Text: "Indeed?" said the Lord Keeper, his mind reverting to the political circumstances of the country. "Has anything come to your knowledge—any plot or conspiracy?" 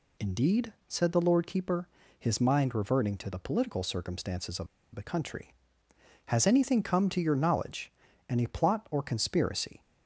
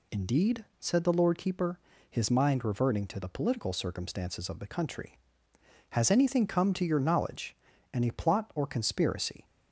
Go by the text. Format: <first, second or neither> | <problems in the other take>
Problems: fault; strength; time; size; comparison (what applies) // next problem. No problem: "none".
second | pauses between "of" and "the"; slight; at 4.6 s; 0.28 s long